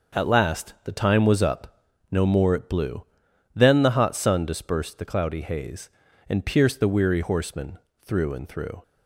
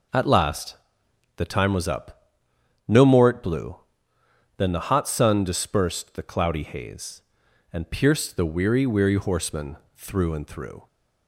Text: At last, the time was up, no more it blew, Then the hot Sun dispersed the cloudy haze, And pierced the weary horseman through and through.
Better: first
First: pauses between "horseman" and "through"; slight; at 7.7 s; 0.24 s long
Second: says "weary" twice; at 8.8 s // pauses between "horseman" and "through"; slight; at 9.7 s; 0.22 s long

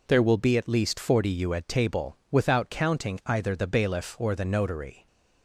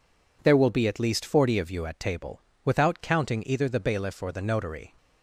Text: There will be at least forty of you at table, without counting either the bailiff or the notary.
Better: second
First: skips "of"; at 1.3 s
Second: none

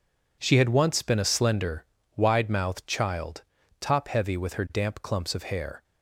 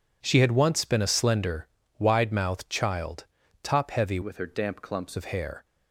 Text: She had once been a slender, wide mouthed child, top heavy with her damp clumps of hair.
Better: first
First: none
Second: changes voice from "with" to "clumps"; from 4.2 to 5.1 s; 0.9 s long

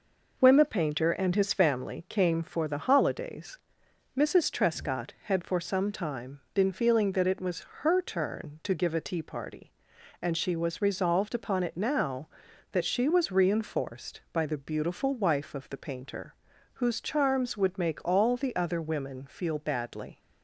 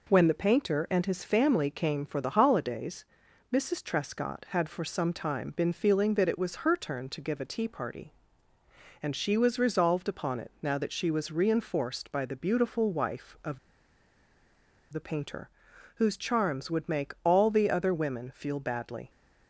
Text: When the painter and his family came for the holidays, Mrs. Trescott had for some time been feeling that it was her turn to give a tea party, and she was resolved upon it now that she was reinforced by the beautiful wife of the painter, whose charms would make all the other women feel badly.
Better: first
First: none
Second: pauses between "of" and "the"; strong; at 13.5 s; 1.3 s long

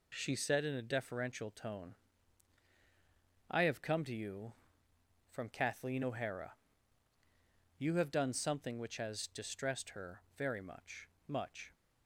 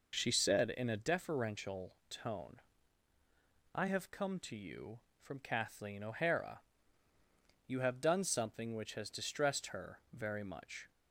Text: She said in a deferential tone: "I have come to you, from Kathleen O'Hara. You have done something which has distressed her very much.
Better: second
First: says "much" twice; at 11.2 s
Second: none

